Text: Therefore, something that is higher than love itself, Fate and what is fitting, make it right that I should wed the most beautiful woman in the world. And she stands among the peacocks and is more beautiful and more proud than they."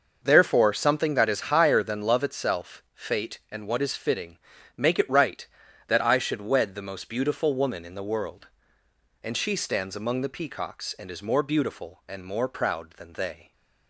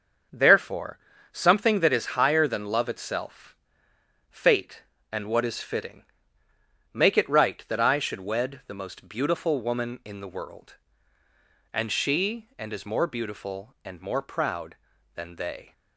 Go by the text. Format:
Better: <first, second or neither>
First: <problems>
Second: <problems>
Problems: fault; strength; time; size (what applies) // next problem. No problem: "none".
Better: first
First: starts louder than the rest; noticeable; until 1.2 s; 6 dB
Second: starts louder than the rest; until 1.6 s; 6.5 dB // skips "stands among the peacocks"; at 12.5 s